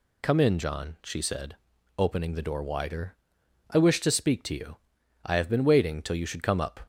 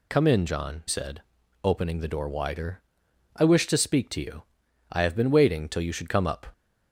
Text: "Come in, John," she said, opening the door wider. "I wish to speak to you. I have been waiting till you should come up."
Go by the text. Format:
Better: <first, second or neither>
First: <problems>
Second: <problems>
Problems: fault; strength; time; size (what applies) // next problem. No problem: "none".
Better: first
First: none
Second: skips "she"; at 0.8 s